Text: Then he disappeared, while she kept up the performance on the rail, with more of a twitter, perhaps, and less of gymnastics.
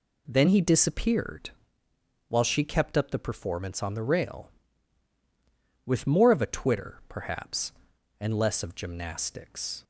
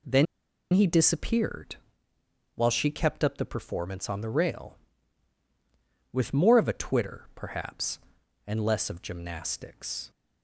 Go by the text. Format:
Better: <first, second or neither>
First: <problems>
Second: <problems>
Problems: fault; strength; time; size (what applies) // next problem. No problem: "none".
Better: first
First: none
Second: pauses between "Then" and "he"; noticeable; at 0.2 s; 0.48 s long